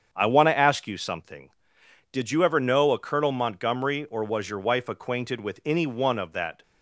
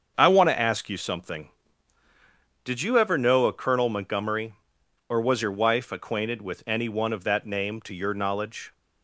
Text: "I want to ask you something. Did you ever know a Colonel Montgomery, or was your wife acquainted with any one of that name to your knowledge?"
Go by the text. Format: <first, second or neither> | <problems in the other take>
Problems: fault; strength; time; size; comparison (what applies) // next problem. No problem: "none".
second | starts louder than the rest; strong; until 1.1 s; 7.5 dB; also in the second // stops before "name to your knowledge"; at 6.6 s